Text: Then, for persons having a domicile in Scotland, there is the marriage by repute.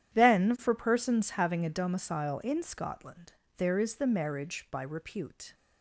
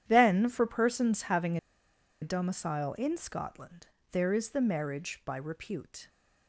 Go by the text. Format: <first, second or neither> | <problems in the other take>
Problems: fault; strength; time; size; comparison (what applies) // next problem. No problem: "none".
first | starts louder than the rest; strong; until 1.0 s; 10 dB; strong in the first // pauses between "having" and "a"; noticeable; at 1.5 s; 0.63 s long